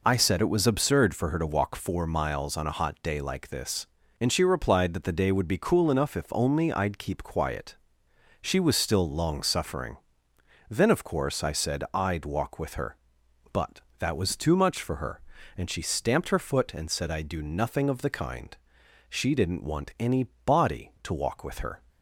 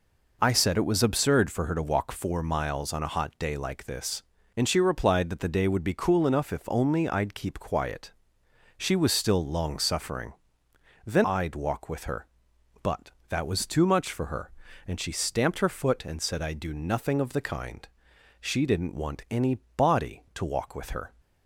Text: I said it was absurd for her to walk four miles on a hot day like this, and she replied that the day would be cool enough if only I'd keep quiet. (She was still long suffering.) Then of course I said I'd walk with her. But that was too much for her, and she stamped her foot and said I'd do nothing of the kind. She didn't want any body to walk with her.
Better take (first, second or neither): first